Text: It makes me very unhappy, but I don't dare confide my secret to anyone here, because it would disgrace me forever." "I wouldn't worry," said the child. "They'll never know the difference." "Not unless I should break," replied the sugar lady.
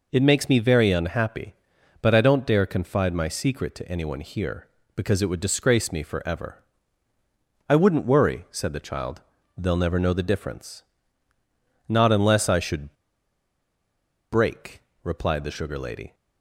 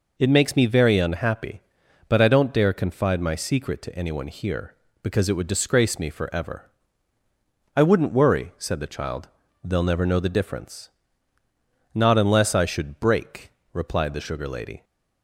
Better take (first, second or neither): second